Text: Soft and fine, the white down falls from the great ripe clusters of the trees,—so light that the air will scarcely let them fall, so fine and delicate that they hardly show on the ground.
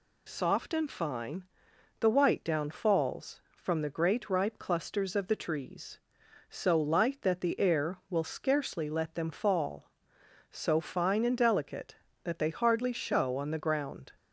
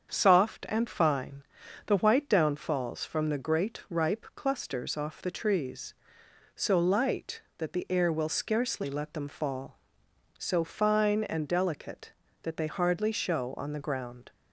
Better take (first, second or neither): first